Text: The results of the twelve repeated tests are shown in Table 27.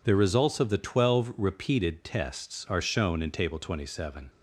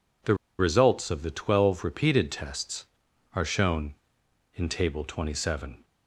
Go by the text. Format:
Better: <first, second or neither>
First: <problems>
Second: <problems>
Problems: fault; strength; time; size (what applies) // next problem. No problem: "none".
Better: first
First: none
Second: pauses between "The" and "results"; slight; at 0.3 s; 0.24 s long